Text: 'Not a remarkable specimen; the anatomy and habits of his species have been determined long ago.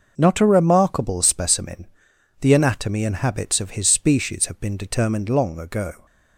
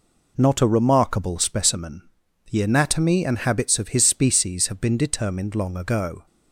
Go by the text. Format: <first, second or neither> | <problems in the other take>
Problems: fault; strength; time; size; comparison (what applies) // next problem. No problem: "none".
neither | none